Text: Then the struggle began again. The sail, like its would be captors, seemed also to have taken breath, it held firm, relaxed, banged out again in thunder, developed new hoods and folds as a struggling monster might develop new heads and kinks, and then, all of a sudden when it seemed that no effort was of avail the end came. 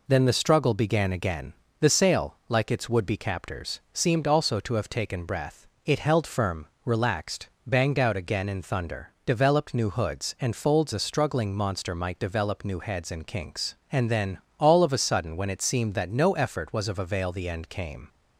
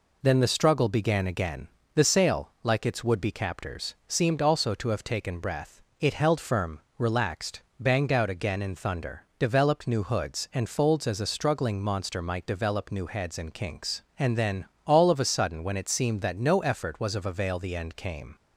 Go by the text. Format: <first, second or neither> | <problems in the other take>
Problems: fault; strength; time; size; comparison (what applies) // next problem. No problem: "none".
second | skips "as"; at 10.9 s